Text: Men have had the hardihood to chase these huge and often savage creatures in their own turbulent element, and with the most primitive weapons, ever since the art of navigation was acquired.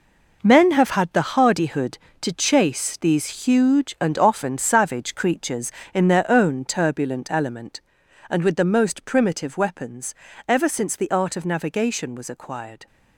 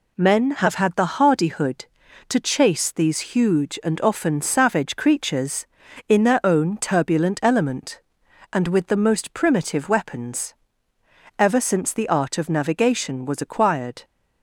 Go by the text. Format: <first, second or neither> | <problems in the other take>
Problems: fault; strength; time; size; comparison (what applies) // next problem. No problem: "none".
second | gets quieter; strong; throughout; 9.5 dB